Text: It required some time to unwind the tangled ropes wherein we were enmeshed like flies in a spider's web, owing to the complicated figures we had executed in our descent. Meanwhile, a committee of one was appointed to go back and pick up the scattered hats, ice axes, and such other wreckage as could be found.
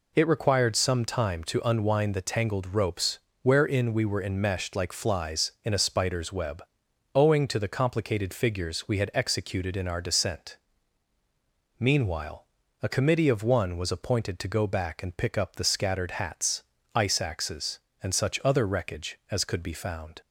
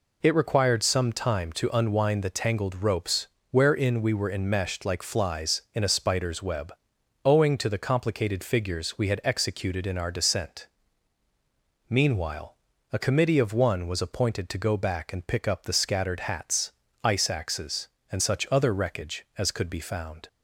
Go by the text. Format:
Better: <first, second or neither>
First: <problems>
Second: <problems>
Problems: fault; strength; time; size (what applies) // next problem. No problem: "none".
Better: neither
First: pauses between "ropes" and "wherein"; slight; at 3.1 s; 0.24 s long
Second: pauses between "ropes" and "wherein"; slight; at 3.2 s; 0.24 s long